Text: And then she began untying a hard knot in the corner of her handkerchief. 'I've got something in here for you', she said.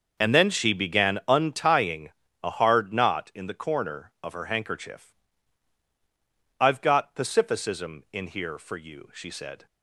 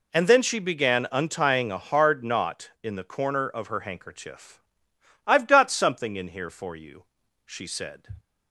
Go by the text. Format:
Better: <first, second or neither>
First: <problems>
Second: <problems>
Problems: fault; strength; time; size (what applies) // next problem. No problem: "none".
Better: second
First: starts louder than the rest; noticeable; until 1.2 s; 6 dB // pauses between "untying" and "a"; slight; at 2.0 s; 0.32 s long // says "pacificism" for "something"; at 7.1 s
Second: none